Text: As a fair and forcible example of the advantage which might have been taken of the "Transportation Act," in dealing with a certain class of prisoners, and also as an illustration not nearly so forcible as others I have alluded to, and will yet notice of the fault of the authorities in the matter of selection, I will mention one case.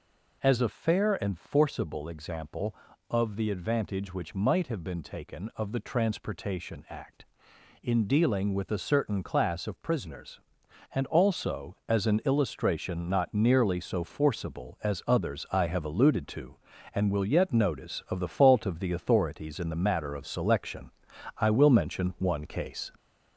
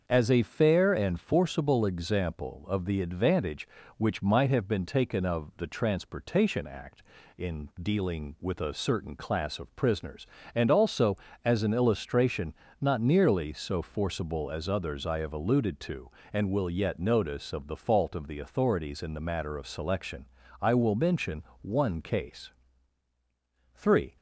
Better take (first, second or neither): first